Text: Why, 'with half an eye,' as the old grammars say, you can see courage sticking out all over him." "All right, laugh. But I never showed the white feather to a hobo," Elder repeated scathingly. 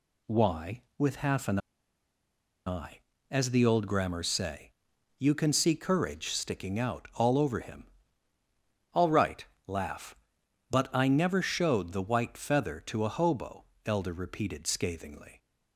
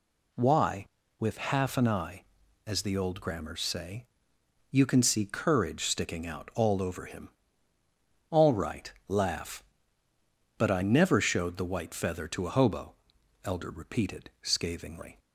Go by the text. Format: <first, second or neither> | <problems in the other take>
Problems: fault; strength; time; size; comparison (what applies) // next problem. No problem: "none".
second | pauses between "an" and "eye"; at 1.5 s; 1.0 s long